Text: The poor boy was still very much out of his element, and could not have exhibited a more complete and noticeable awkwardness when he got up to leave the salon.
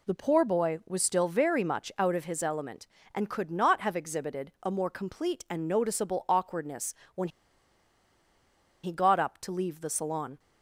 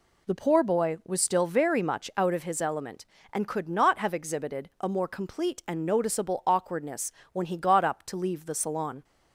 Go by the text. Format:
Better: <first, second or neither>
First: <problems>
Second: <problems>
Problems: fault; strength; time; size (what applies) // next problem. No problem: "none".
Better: second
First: pauses between "awkwardness" and "when"; slight; at 6.9 s; 0.22 s long // pauses between "when" and "he"; strong; at 7.2 s; 1.5 s long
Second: pauses between "awkwardness" and "when"; slight; at 7.0 s; 0.22 s long